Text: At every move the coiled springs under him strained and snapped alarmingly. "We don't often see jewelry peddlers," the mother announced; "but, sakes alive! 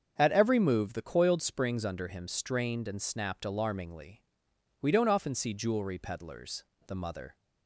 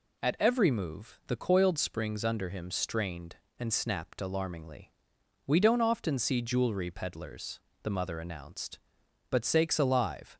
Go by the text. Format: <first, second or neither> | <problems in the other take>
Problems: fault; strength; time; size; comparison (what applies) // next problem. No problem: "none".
second | starts louder than the rest; until 1.1 s; 7 dB // stops before "announced but sakes alive"; at 7.3 s